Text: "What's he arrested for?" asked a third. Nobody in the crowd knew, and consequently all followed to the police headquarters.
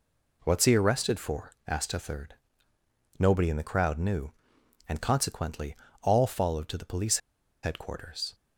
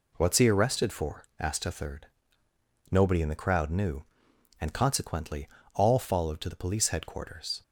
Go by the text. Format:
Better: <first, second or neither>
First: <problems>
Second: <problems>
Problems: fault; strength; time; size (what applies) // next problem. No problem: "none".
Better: second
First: pauses between "consequently" and "all"; slight; at 5.7 s; 0.26 s long // pauses between "police" and "headquarters"; at 7.1 s; 0.45 s long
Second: pauses between "consequently" and "all"; slight; at 5.4 s; 0.26 s long